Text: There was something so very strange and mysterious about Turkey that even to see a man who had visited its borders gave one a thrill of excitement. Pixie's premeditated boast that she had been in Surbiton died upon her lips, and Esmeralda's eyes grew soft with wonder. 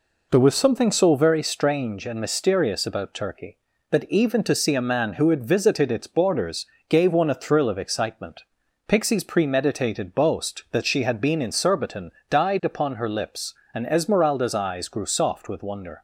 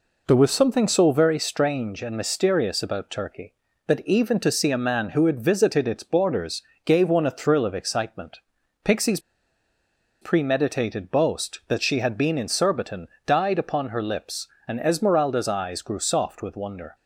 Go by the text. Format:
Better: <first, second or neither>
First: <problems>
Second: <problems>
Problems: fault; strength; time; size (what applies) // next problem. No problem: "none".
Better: first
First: pauses between "borders" and "gave"; slight; at 6.6 s; 0.24 s long // pauses between "Surbiton" and "died"; slight; at 12.1 s; 0.18 s long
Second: pauses between "borders" and "gave"; slight; at 6.6 s; 0.24 s long // pauses between "Pixie's" and "premeditated"; at 9.1 s; 1.0 s long // pauses between "Surbiton" and "died"; slight; at 13.0 s; 0.18 s long